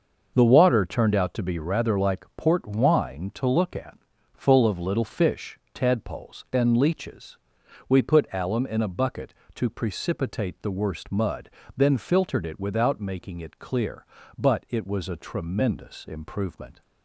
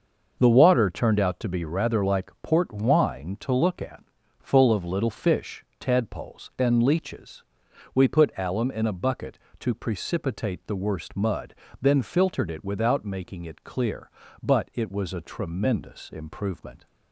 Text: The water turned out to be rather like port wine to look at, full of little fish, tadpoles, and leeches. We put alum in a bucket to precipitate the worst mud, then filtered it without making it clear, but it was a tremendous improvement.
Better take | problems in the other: neither | starts louder than the rest; the same in both

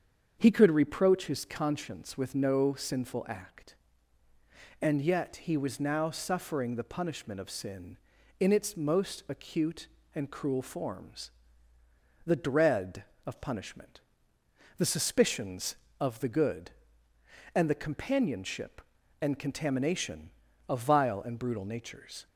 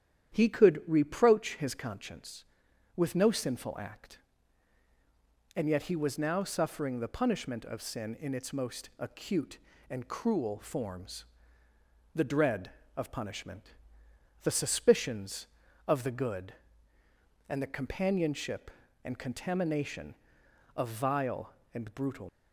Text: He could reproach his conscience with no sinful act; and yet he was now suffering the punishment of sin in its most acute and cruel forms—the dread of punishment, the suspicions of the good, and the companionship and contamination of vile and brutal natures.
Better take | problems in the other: first | starts louder than the rest; strong; until 1.3 s; 9.5 dB; strong in the first // stops before "natures"; at 22.2 s

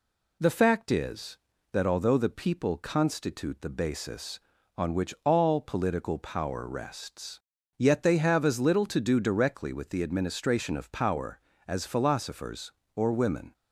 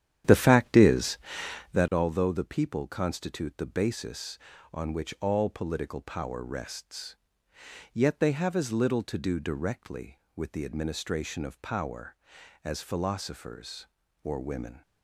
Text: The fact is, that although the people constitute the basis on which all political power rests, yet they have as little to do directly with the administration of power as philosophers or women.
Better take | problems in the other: first | starts louder than the rest; strong; until 1.9 s; 10.5 dB

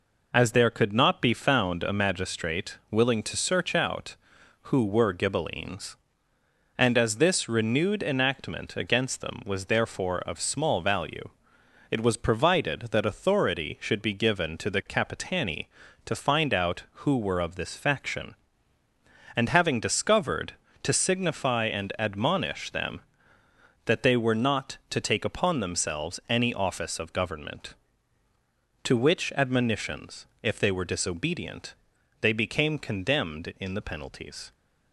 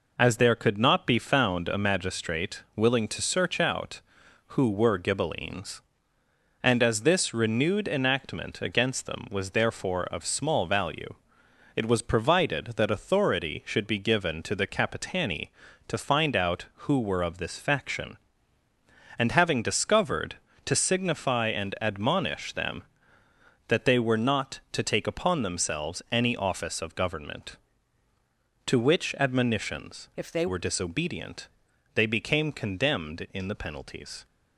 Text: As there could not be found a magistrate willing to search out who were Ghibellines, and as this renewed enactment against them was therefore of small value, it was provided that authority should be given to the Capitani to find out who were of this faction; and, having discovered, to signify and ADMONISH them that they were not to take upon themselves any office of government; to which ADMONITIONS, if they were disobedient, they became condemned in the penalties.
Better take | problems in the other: first | changes voice from "if" to "they"; from 30.1 to 30.4 s; 0.3 s long

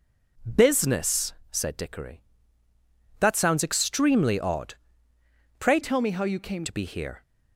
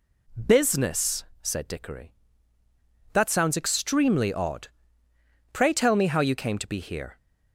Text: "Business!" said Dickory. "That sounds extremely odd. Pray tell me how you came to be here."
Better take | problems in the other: second | changes voice from "tell" to "came"; from 5.8 to 6.6 s; 0.8 s long

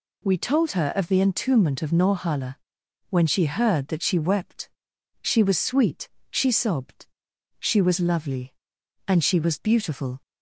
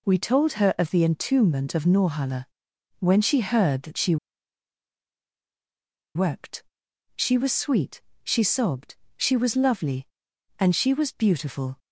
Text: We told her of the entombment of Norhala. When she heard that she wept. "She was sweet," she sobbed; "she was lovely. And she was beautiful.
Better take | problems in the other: first | pauses between "she" and "wept"; strong; at 4.1 s; 1.9 s long

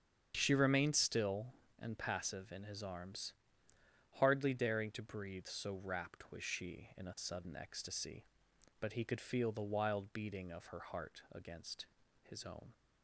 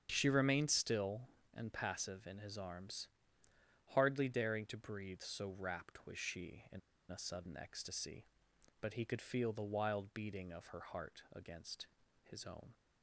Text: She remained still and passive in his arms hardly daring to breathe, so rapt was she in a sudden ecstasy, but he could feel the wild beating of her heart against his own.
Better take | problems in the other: first | starts louder than the rest; strong; until 1.1 s; 8 dB; strong in the first // pauses between "arms" and "hardly"; noticeable; at 3.0 s; 0.88 s long; noticeable in the first // pauses between "in" and "a"; slight; at 6.8 s; 0.31 s long // pauses between "against" and "his"; slight; at 11.8 s; 0.36 s long; slight in the first

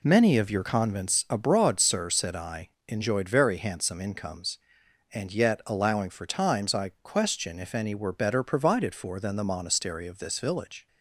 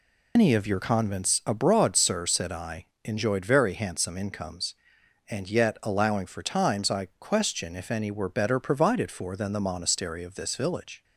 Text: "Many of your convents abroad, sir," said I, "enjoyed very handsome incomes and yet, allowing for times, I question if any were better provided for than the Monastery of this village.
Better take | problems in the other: first | loses the start of "Many"; at 0.3 s; 150 ms

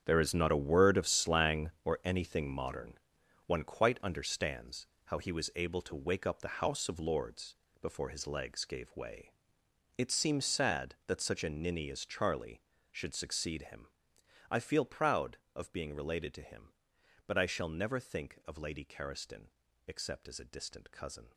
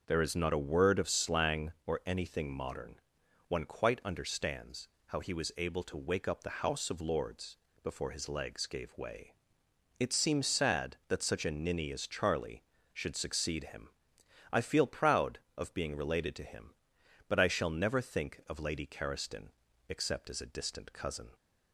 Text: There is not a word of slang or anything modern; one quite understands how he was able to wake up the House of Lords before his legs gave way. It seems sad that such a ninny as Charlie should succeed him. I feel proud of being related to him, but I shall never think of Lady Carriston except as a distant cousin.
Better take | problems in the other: second | gets quieter; strong; throughout; 12.5 dB // starts louder than the rest; strong; until 1.0 s; 8 dB; noticeable in the second // pauses between "understands" and "how"; slight; at 4.8 s; 0.20 s long; slight in the second // pauses between "Lords" and "before"; slight; at 7.5 s; 0.26 s long; slight in the second // pauses between "Carriston" and "except"; at 19.4 s; 0.40 s long; also in the second

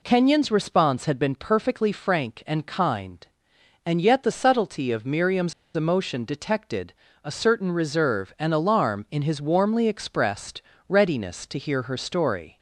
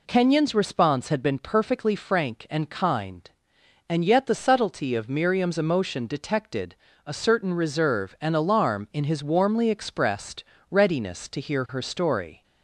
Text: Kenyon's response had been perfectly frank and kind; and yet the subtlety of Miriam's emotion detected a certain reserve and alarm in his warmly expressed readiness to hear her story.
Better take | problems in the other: second | pauses between "Miriam's" and "emotion"; slight; at 5.5 s; 0.22 s long // pauses between "detected" and "a"; slight; at 6.9 s; 0.28 s long; slight in the second // pauses between "expressed" and "readiness"; slight; at 10.6 s; 0.26 s long; slight in the second

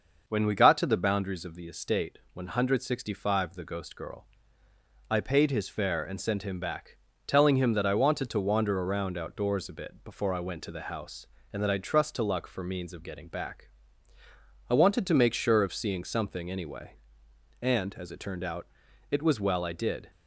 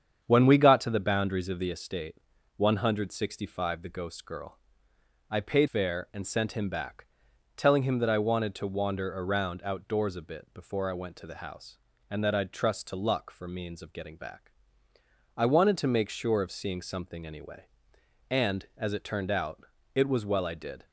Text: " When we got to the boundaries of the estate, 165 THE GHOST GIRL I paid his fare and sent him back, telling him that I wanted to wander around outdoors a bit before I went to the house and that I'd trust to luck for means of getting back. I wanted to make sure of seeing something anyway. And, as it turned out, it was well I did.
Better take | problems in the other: first | starts louder than the rest; strong; until 1.2 s; 8 dB; noticeable in the first // pauses between "GIRL" and "I"; noticeable; at 4.5 s; 0.72 s long; noticeable in the first // skips "his"; at 5.6 s

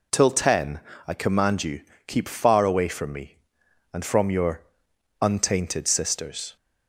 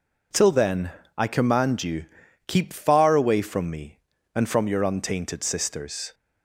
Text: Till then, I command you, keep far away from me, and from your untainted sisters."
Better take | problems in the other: second | says "ten" for "then"; at 0.3 s // pauses between "your" and "untainted"; noticeable; at 4.6 s; 0.60 s long

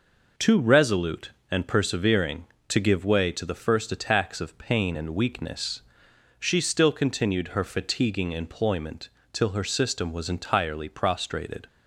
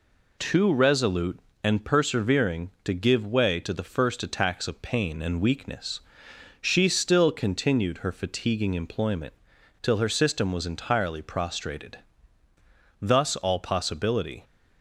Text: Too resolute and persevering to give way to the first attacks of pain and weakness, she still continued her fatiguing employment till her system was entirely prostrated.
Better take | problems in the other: first | pauses between "employment" and "till"; noticeable; at 9.3 s; 0.49 s long; slight in the first // goes on to say "Thus all possibility"; from 12.9 s on; 1.4 s long

